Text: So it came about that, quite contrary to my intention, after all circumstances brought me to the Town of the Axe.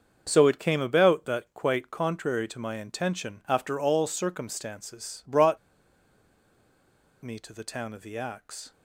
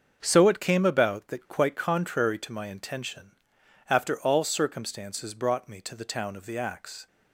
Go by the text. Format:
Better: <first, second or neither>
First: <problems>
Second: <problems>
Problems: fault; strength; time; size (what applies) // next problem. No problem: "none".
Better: second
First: starts louder than the rest; until 1.2 s; 6.5 dB // pauses between "brought" and "me"; strong; at 5.5 s; 1.6 s long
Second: starts louder than the rest; until 1.2 s; 6.5 dB